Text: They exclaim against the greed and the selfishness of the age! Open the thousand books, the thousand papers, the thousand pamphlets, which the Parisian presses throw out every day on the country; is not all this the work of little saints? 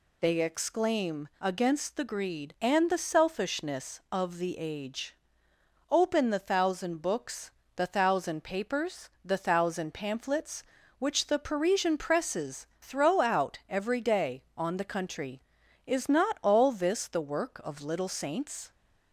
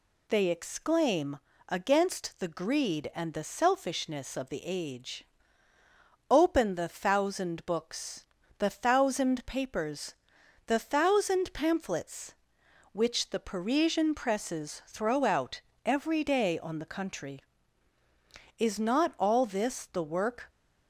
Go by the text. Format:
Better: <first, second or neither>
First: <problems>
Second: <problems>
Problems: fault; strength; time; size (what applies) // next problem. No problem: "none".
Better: first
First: none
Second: pauses between "exclaim" and "against"; slight; at 1.3 s; 0.30 s long // pauses between "out" and "every"; slight; at 15.6 s; 0.24 s long // stops before "of little saints"; at 20.4 s